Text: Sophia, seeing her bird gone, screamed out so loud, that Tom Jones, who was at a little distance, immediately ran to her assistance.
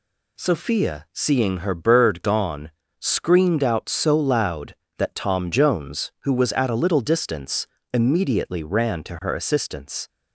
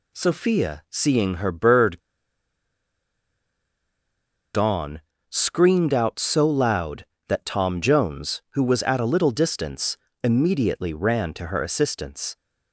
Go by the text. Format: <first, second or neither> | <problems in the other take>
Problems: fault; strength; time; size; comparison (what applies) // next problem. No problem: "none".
first | pauses between "bird" and "gone"; strong; at 1.9 s; 2.5 s long